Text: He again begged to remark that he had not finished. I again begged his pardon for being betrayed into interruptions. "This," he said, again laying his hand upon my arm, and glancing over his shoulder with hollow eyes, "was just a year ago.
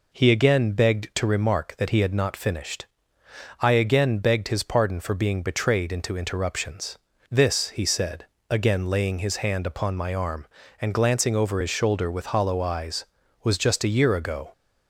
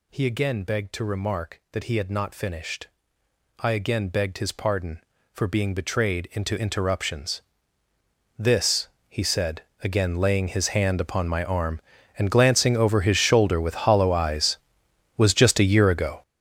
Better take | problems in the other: first | gets louder; strong; throughout; 13.5 dB

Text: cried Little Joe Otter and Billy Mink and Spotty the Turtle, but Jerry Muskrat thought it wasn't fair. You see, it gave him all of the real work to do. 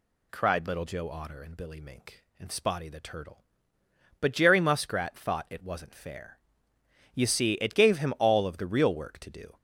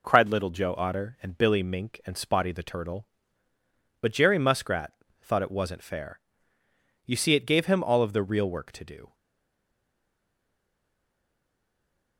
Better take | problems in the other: first | pauses between "Muskrat" and "thought"; slight; at 4.9 s; 0.28 s long // stays silent after the last word; strong; from 9.1 s on; 3.0 s long

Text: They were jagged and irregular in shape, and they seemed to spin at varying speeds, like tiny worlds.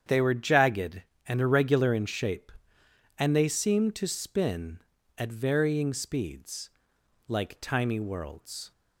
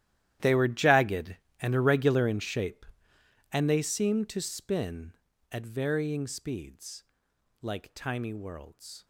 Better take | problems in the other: first | gets quieter; strong; throughout; 18 dB // starts louder than the rest; strong; until 1.6 s; 12.5 dB; strong in the first

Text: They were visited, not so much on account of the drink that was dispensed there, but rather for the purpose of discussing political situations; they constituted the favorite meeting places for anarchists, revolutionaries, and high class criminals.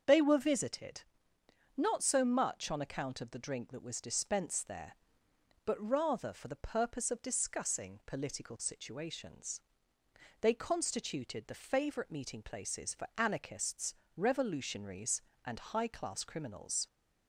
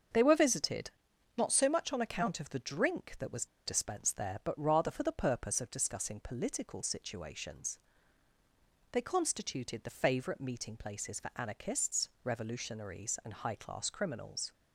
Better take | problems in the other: first | starts louder than the rest; strong; until 1.5 s; 7 dB; also in the first // pauses between "was" and "dispensed"; slight; at 3.4 s; 0.19 s long

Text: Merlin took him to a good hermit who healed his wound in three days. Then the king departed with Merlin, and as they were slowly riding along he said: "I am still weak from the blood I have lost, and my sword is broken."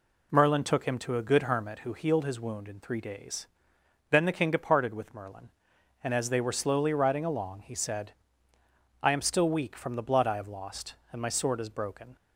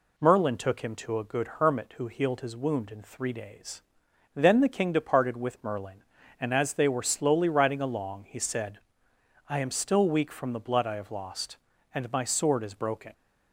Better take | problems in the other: neither | none

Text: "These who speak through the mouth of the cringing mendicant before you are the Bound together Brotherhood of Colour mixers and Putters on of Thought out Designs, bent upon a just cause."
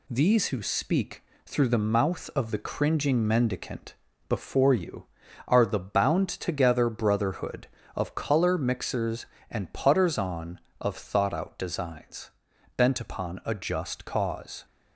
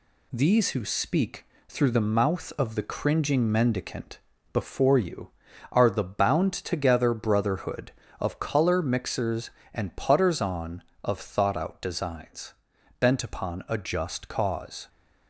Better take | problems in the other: neither | pauses between "speak" and "through"; slight; the same in both // pauses between "mendicant" and "before"; slight; the same in both

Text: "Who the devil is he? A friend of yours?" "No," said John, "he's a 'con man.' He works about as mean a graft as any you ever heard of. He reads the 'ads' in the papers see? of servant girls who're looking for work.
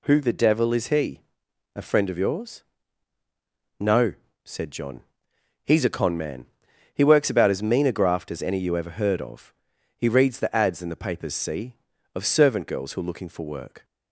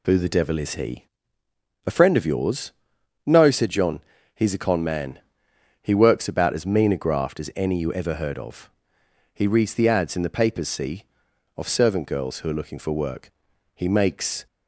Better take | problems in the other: first | goes on to say "He makes"; noticeable; from 13.7 s on; 0.72 s long

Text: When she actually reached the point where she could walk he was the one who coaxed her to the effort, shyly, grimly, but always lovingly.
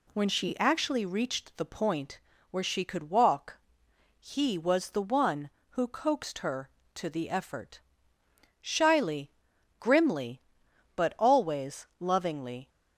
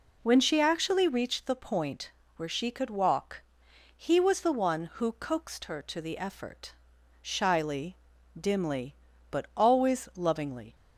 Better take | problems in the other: first | pauses between "point" and "where"; slight; at 2.1 s; 0.24 s long; slight in the first // pauses between "walk" and "he"; noticeable; at 3.4 s; 0.54 s long; noticeable in the first // says "dimly" for "grimly"; at 8.3 s

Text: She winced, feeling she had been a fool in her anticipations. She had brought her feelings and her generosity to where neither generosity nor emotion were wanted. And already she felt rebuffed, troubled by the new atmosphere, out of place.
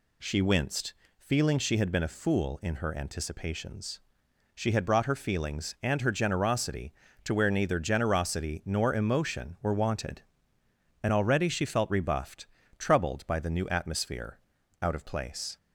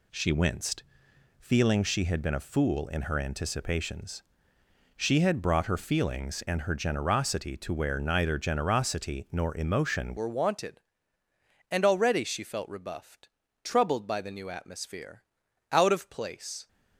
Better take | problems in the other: first | changes voice at "were"; from 10.1 s on; 6.5 s long

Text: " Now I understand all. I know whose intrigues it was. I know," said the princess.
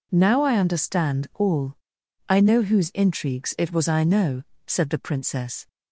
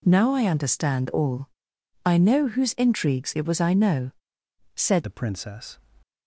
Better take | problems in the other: first | changes voice at "the"; from 5.0 s on; 0.7 s long

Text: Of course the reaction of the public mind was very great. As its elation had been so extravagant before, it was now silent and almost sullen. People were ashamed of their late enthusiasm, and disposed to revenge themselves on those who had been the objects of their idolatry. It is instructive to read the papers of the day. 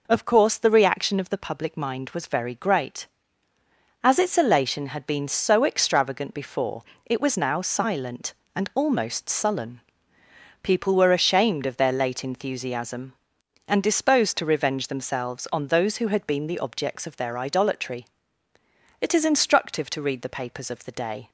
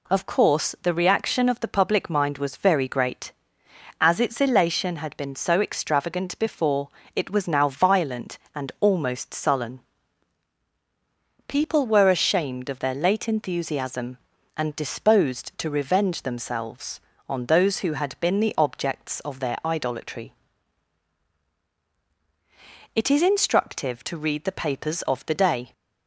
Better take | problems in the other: first | says "violent" for "silent"; at 7.6 s

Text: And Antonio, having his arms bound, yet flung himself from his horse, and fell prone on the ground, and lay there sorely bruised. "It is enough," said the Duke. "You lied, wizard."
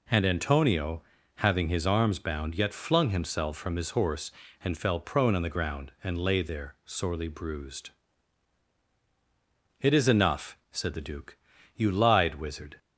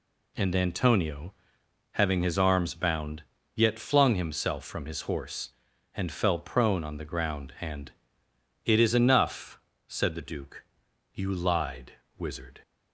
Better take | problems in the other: first | skips "lay there sorely bruised"; at 8.2 s

